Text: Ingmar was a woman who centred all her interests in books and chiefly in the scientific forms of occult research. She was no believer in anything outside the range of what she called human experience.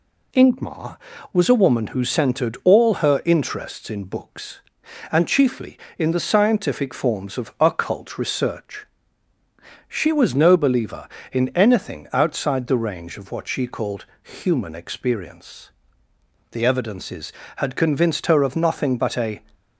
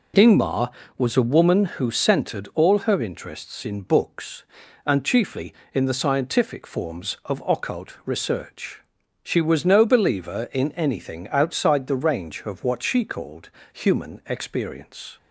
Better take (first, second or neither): second